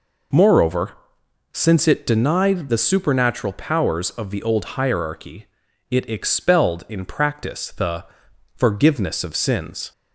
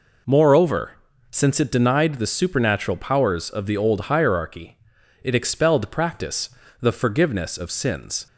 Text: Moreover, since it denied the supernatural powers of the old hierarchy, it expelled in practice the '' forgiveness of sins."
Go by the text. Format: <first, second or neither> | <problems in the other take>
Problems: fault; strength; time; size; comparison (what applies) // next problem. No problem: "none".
first | skips "in"; at 5.9 s // pauses between "practice" and "the"; slight; at 6.5 s; 0.30 s long